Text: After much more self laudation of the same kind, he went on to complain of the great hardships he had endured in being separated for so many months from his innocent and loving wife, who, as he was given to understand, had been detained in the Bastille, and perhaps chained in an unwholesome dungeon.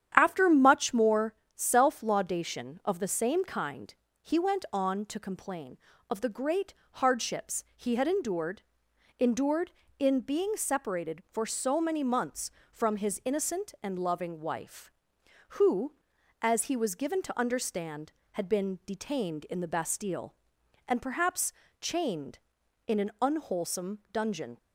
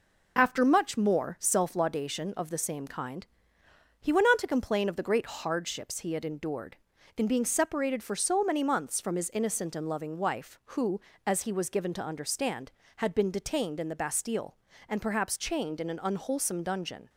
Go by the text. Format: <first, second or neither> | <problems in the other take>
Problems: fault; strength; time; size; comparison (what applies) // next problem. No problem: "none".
second | starts louder than the rest; strong; until 1.1 s; 9.5 dB // pauses between "more" and "self"; slight; at 1.3 s; 0.22 s long // pauses between "great" and "hardships"; slight; at 6.7 s; 0.20 s long // says "endured" twice; at 9.1 s // pauses between "perhaps" and "chained"; slight; at 21.5 s; 0.26 s long